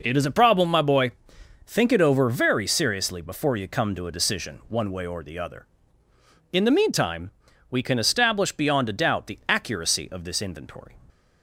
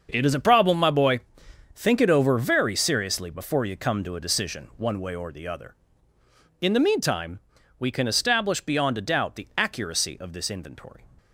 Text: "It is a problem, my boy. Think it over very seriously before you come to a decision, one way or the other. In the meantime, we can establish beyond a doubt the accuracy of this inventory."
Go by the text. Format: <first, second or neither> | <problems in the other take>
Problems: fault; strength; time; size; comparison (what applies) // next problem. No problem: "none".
first | gets quieter; strong; throughout; 12.5 dB